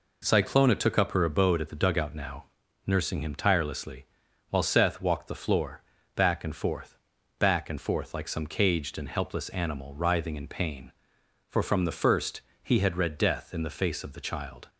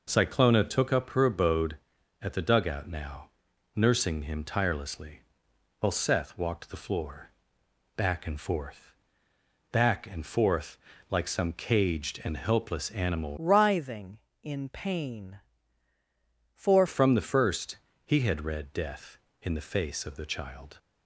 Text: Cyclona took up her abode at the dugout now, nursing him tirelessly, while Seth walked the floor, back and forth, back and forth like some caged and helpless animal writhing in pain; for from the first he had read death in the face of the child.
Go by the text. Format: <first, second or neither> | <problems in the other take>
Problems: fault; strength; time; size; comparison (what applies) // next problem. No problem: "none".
first | pauses between "forth" and "like"; slight; at 10.7 s; 0.32 s long // changes voice from "writhing" to "for"; from 13.3 to 16.8 s; 3.5 s long // pauses between "first" and "he"; slight; at 17.7 s; 0.30 s long; slight in the first